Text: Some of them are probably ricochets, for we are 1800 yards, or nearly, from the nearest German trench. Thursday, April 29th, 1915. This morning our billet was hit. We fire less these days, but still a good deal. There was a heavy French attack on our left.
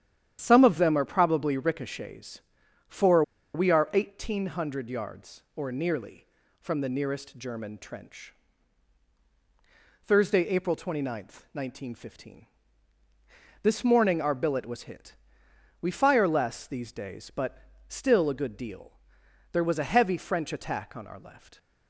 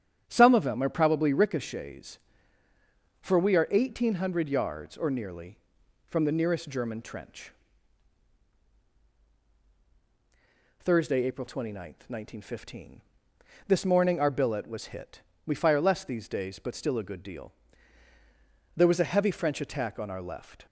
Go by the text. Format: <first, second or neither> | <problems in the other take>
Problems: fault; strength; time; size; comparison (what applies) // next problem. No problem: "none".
second | starts louder than the rest; strong; until 1.4 s; 10 dB; strong in the second // pauses between "for" and "we"; slight; at 3.2 s; 0.32 s long // pauses between "but" and "still"; slight; at 17.5 s; 0.30 s long